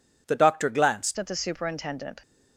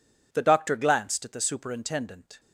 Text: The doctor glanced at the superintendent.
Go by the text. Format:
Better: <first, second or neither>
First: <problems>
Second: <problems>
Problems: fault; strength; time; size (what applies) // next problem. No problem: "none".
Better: second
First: changes voice at "at"; from 1.1 s on; 1.1 s long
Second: none